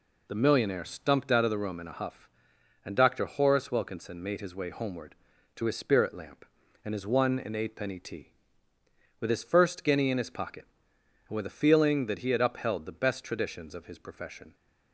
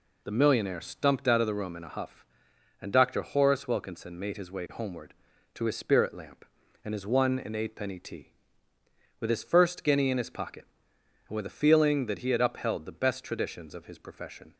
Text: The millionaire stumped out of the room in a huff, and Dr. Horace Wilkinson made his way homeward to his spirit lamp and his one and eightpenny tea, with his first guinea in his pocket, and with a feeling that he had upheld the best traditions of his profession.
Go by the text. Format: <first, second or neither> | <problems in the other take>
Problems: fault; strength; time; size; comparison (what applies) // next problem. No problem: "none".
neither | none